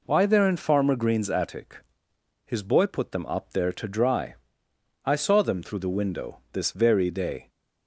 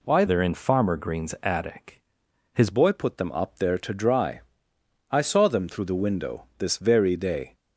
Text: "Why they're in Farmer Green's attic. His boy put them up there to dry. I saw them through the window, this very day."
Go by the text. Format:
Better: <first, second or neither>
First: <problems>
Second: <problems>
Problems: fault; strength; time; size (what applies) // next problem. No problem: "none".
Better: first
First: none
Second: changes voice from "they're" to "His"; from 0.2 to 2.6 s; 2.4 s long